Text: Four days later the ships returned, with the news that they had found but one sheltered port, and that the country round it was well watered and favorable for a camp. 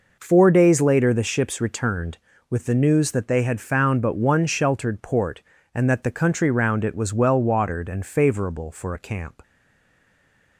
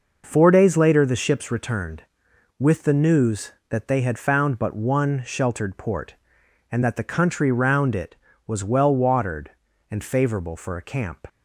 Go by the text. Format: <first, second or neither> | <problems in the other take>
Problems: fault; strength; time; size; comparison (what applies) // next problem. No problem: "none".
second | stays silent after the last word; noticeable; from 9.4 s on; 1.1 s long